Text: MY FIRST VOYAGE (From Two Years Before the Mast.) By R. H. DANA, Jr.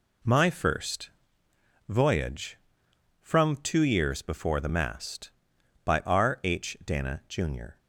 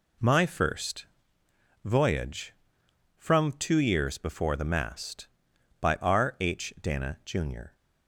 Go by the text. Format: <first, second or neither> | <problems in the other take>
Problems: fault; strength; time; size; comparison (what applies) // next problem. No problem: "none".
neither | pauses between "FIRST" and "VOYAGE"; noticeable; the same in both